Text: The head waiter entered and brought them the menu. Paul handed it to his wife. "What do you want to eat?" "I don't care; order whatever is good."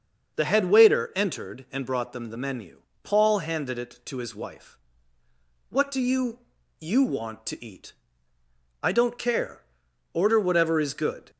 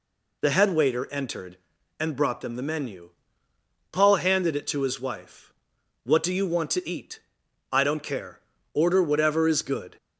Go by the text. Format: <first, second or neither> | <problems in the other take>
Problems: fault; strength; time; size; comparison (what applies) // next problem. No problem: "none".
second | starts louder than the rest; until 1.4 s; 6 dB // says "you" twice; at 6.8 s